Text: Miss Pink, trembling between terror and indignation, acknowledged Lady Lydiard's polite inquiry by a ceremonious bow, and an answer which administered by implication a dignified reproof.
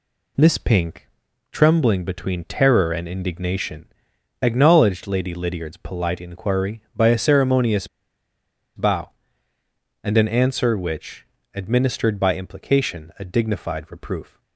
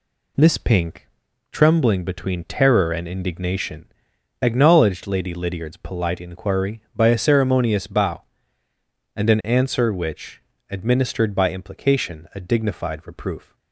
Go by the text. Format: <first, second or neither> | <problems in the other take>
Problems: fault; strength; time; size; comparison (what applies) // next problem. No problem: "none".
second | pauses between "ceremonious" and "bow"; noticeable; at 7.8 s; 0.88 s long // pauses between "which" and "administered"; slight; at 11.2 s; 0.30 s long; slight in the second